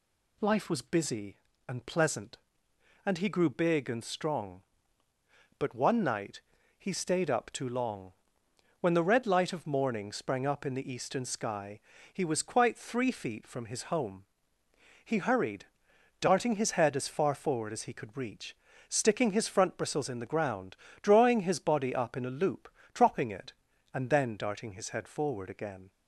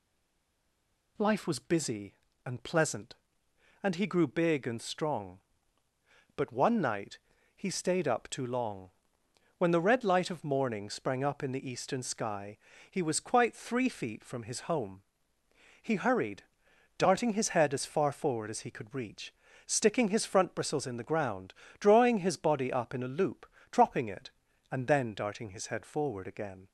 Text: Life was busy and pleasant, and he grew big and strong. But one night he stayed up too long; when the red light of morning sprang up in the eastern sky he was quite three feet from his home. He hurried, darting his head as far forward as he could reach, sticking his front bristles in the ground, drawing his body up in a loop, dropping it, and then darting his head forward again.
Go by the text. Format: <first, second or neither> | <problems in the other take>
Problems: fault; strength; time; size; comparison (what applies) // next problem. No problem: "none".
first | stays silent before the first word; noticeable; until 1.1 s; 1.1 s long // pauses between "night" and "he"; slight; at 7.1 s; 0.36 s long; slight in the first // pauses between "sky" and "he"; slight; at 12.5 s; 0.34 s long; slight in the first